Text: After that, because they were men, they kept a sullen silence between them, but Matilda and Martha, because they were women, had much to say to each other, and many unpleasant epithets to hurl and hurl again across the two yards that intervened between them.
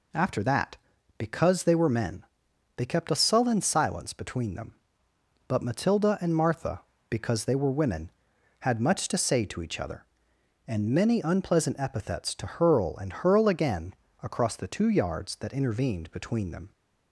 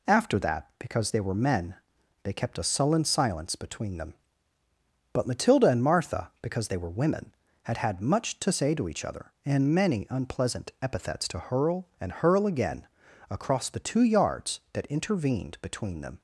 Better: first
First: pauses between "again" and "across"; slight; at 13.9 s; 0.30 s long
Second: says "had" twice; at 7.7 s // pauses between "again" and "across"; at 12.8 s; 0.44 s long

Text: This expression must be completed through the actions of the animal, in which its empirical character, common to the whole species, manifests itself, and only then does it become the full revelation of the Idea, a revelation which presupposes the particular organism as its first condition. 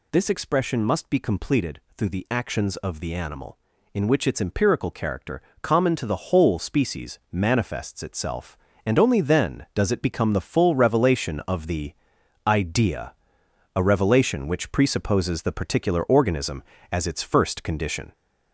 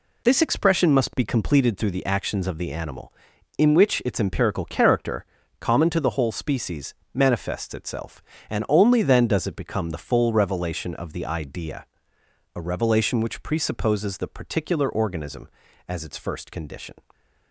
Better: second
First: gets louder; throughout; 3.5 dB // pauses between "completed" and "through"; slight; at 1.7 s; 0.16 s long // pauses between "the" and "Idea"; noticeable; at 11.9 s; 0.54 s long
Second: none

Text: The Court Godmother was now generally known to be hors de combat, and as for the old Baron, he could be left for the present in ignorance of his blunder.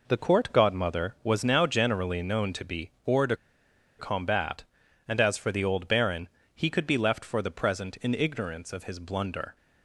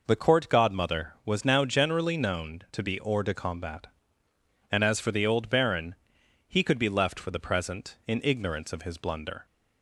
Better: second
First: pauses between "be" and "hors"; slight; at 2.9 s; 0.16 s long // pauses between "de" and "combat"; noticeable; at 3.3 s; 0.63 s long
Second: none

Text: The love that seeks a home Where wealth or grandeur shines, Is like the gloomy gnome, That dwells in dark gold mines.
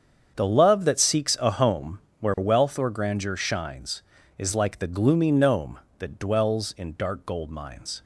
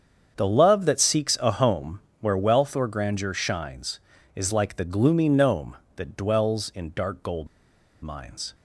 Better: first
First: starts louder than the rest; strong; until 1.3 s; 7.5 dB // pauses between "home" and "Where"; slight; at 1.9 s; 0.20 s long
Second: starts louder than the rest; strong; until 1.3 s; 7.5 dB // pauses between "home" and "Where"; slight; at 2.0 s; 0.20 s long // pauses between "gold" and "mines"; noticeable; at 7.4 s; 0.55 s long

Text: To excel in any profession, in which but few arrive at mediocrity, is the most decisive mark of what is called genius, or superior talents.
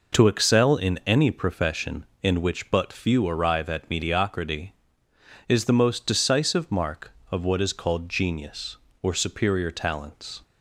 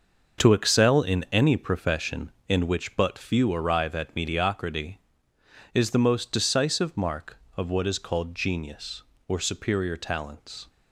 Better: first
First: none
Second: gets quieter; strong; throughout; 9.5 dB

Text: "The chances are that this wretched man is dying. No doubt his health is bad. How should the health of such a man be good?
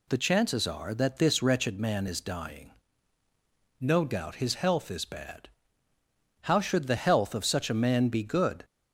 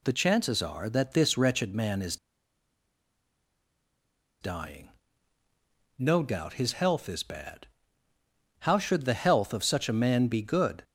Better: first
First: none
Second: pauses between "is" and "dying"; strong; at 2.1 s; 2.2 s long

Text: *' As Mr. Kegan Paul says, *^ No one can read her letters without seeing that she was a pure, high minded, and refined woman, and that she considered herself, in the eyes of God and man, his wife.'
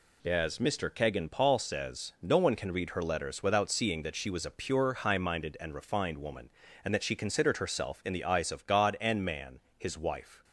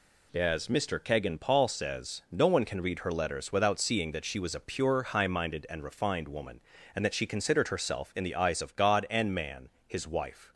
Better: neither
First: none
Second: none

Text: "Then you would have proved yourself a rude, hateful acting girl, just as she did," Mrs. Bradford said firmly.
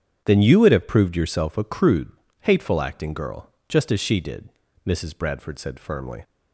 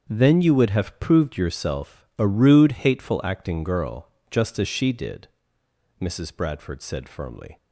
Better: second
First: starts louder than the rest; strong; until 1.2 s; 8 dB // says "crude" for "rude"; at 1.6 s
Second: starts louder than the rest; strong; until 1.1 s; 7.5 dB

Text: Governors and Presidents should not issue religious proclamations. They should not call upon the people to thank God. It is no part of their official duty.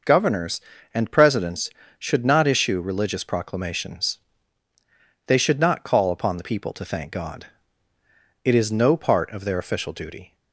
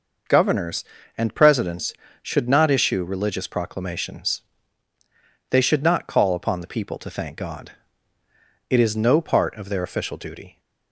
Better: neither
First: none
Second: none

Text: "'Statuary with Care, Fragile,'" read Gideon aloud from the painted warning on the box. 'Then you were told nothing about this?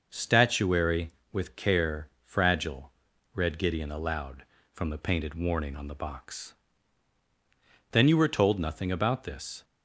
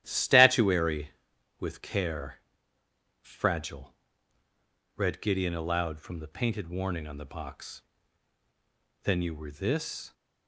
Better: first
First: none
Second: starts louder than the rest; strong; until 1.0 s; 12 dB // skips "told nothing about"; at 9.4 s

